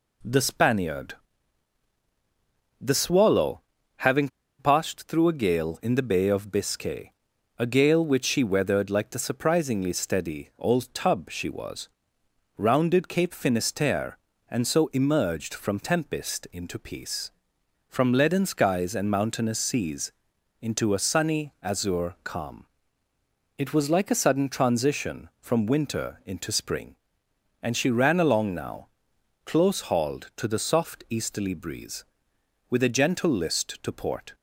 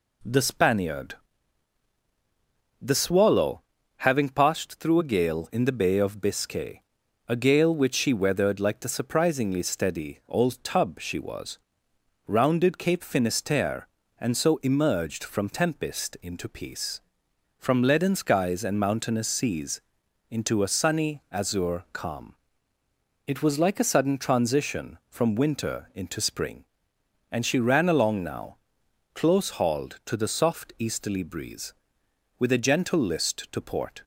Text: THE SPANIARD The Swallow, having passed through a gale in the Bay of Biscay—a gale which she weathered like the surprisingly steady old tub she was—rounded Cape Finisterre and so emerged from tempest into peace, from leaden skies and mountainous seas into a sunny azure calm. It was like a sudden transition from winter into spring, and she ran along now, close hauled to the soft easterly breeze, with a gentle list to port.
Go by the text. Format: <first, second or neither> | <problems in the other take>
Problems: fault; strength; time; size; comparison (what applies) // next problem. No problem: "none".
second | pauses between "SPANIARD" and "The"; strong; at 1.1 s; 1.6 s long; strong in the second // pauses between "having" and "passed"; slight; at 4.2 s; 0.31 s long // pauses between "seas" and "into"; noticeable; at 20.1 s; 0.50 s long; noticeable in the second